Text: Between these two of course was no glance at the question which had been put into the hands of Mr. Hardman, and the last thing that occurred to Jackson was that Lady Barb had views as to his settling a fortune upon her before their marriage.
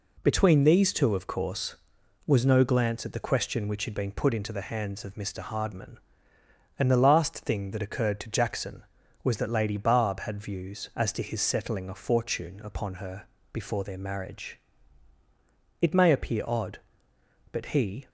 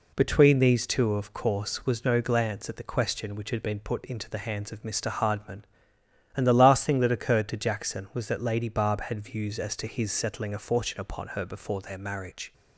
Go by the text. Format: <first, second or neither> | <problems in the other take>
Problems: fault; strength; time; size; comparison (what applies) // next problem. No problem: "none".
second | pauses between "her" and "before"; slight; at 13.2 s; 0.26 s long // goes on to say "It may appear odd but he"; strong; from 15.8 s on; 2.2 s long